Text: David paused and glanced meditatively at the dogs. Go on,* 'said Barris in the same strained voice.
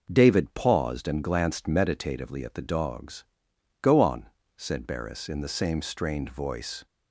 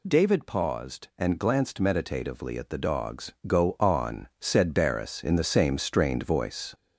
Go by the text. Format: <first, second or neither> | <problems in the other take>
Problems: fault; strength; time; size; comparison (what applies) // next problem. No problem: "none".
first | gets louder; noticeable; throughout; 4 dB